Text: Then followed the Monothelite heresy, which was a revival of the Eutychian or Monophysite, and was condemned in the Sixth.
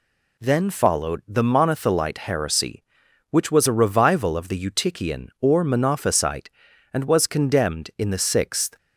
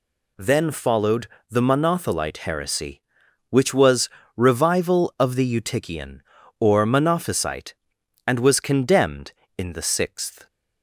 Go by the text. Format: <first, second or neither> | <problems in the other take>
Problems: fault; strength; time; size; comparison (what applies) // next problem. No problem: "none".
first | pauses between "followed" and "the"; slight; at 1.2 s; 0.24 s long // skips "a"; at 4.2 s